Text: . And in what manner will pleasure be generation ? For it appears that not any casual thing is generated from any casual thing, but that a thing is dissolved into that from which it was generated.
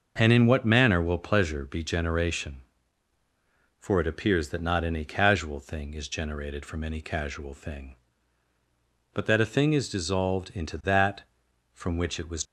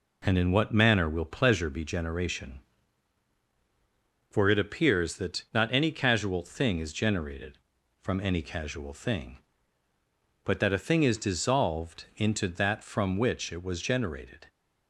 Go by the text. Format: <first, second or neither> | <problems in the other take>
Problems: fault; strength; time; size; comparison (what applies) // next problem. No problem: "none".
second | starts louder than the rest; until 1.1 s; 6 dB // stops before "generated"; at 12.4 s